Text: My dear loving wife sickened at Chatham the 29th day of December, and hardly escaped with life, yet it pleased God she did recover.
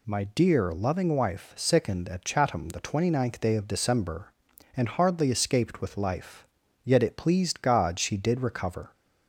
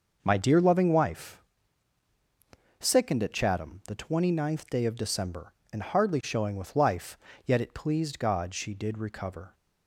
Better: first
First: none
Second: pauses between "wife" and "sickened"; strong; at 1.4 s; 1.3 s long // says "showing" for "escaped"; at 6.2 s

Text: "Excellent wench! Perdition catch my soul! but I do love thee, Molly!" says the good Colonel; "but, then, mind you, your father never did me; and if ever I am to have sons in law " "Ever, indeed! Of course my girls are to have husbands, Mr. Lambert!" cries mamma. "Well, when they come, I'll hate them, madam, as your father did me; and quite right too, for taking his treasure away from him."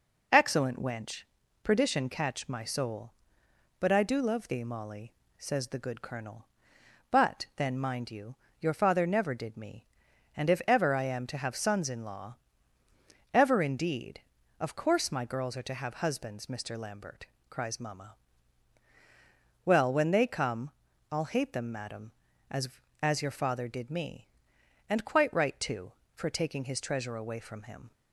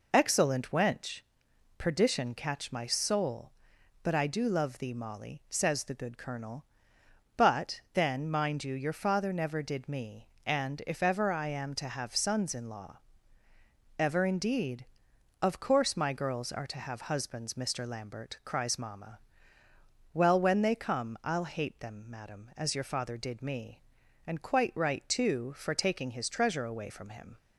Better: second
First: says "as" twice; at 22.9 s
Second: none

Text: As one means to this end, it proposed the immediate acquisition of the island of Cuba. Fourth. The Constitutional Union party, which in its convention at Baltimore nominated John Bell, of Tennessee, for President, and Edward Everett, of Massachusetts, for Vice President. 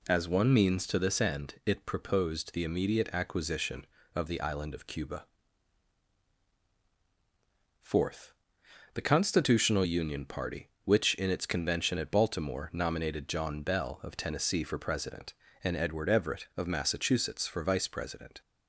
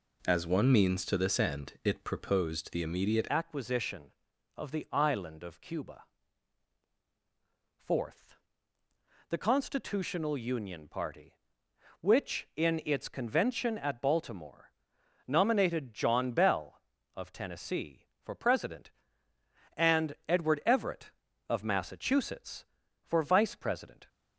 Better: first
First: none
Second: changes voice at "acquisition"; from 3.2 s on; 20.8 s long // pauses between "Baltimore" and "nominated"; noticeable; at 14.7 s; 0.56 s long

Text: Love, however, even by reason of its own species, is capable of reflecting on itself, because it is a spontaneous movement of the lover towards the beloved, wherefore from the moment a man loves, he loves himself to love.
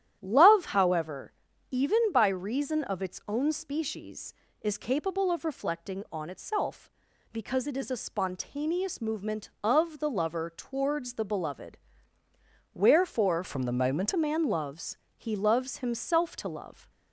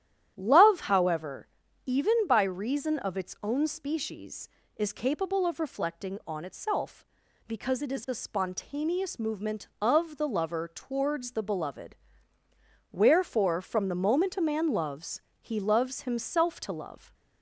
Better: second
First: starts louder than the rest; strong; until 1.2 s; 10.5 dB // changes voice from "from" to "moment"; from 13.4 to 14.1 s; 0.7 s long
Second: starts louder than the rest; strong; until 1.3 s; 10.5 dB

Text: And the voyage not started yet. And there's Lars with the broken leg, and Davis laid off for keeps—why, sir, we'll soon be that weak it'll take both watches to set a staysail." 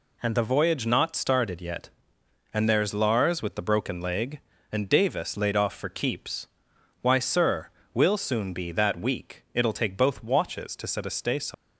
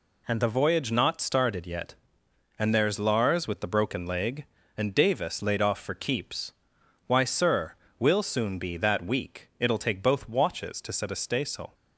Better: second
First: leaves "staysail" unfinished; at 11.5 s; 140 ms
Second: none

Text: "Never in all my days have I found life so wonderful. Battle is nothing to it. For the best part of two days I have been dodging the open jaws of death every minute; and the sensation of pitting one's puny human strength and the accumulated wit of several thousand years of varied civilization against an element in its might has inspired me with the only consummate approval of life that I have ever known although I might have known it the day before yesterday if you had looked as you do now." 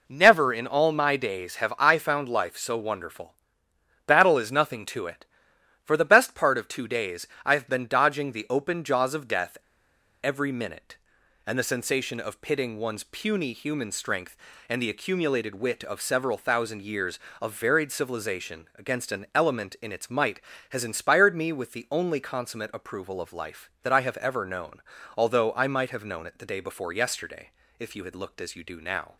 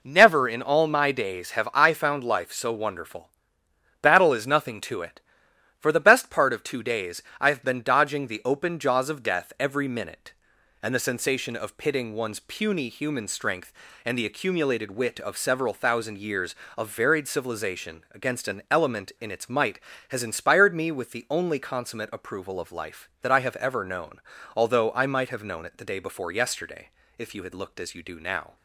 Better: second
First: pauses between "days" and "I"; slight; at 7.2 s; 0.18 s long // pauses between "death" and "every"; noticeable; at 9.5 s; 0.67 s long // pauses between "known" and "although"; slight; at 24.8 s; 0.34 s long // pauses between "yesterday" and "if"; slight; at 27.5 s; 0.28 s long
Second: pauses between "days" and "I"; slight; at 7.2 s; 0.18 s long // pauses between "known" and "although"; slight; at 24.1 s; 0.34 s long // pauses between "yesterday" and "if"; slight; at 26.8 s; 0.28 s long

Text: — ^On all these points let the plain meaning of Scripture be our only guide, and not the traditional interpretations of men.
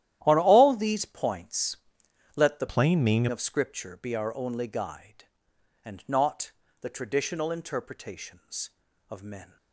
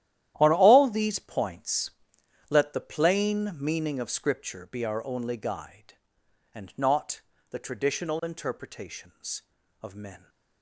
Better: second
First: starts louder than the rest; strong; until 1.2 s; 12 dB // pauses between "points" and "let"; noticeable; at 1.7 s; 0.58 s long // changes voice from "plain" to "meaning"; from 2.6 to 3.2 s; 0.6 s long // pauses between "not" and "the"; slight; at 6.5 s; 0.28 s long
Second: starts louder than the rest; strong; until 1.4 s; 12 dB // pauses between "points" and "let"; noticeable; at 1.9 s; 0.58 s long // pauses between "not" and "the"; slight; at 7.2 s; 0.28 s long

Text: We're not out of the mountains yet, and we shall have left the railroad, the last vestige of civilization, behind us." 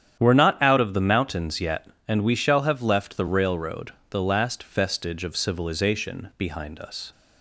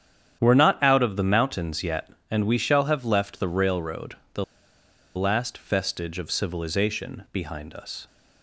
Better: first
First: starts louder than the rest; strong; until 1.2 s; 9.5 dB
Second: starts louder than the rest; strong; until 1.4 s; 9 dB // pauses between "the" and "last"; noticeable; at 4.4 s; 0.73 s long

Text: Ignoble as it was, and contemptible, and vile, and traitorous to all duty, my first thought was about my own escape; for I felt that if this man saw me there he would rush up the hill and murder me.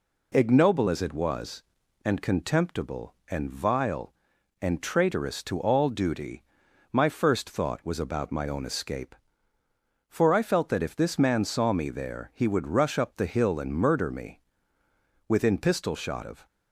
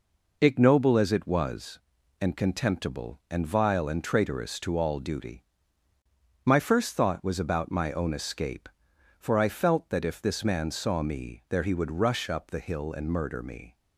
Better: second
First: goes on to say "Within pistol shot of"; noticeable; from 15.2 s on; 1.1 s long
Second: none

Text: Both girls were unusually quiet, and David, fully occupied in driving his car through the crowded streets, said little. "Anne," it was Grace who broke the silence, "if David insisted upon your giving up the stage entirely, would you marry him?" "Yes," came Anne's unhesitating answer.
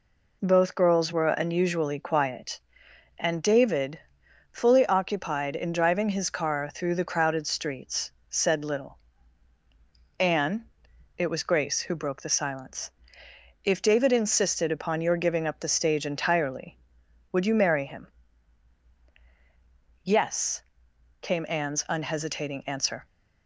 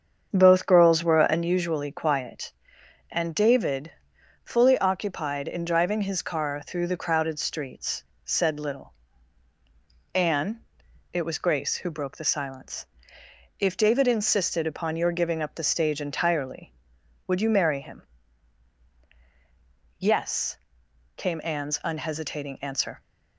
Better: first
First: none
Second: starts louder than the rest; strong; until 1.5 s; 7.5 dB

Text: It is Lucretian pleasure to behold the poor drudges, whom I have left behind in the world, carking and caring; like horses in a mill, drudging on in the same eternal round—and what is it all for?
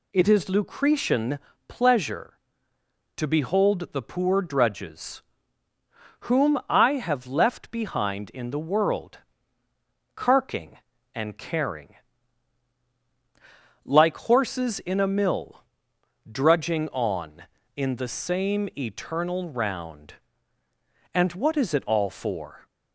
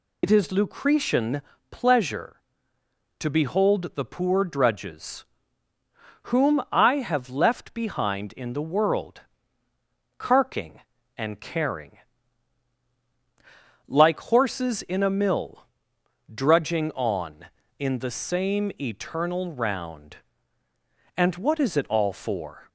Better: first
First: pauses between "Lucretian" and "pleasure"; slight; at 1.3 s; 0.30 s long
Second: loses the start of "It"; at 0.2 s; 70 ms // pauses between "Lucretian" and "pleasure"; slight; at 1.4 s; 0.30 s long

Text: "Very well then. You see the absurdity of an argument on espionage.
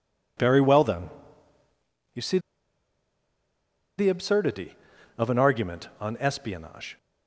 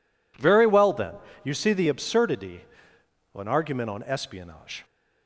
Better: second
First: pauses between "see" and "the"; strong; at 2.3 s; 1.5 s long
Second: none

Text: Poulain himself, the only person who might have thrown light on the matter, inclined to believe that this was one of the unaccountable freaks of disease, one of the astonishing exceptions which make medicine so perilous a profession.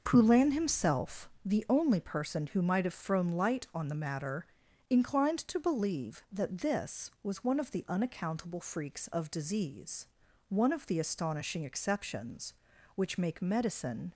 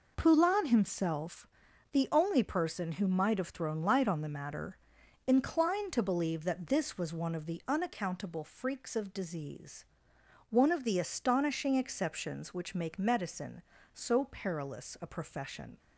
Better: second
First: stops before "so perilous a profession"; at 14.1 s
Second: none

